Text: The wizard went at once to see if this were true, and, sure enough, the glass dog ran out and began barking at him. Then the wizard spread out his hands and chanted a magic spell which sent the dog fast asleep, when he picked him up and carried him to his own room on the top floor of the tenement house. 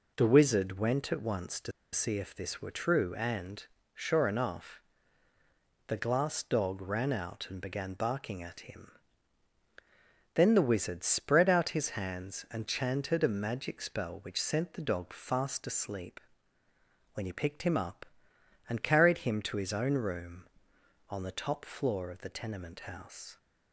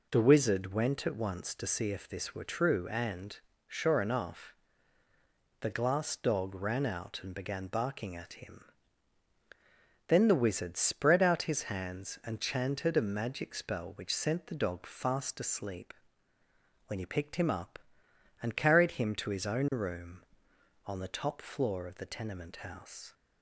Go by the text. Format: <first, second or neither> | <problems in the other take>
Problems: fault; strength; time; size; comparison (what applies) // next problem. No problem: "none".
second | pauses between "to" and "see"; slight; at 1.7 s; 0.21 s long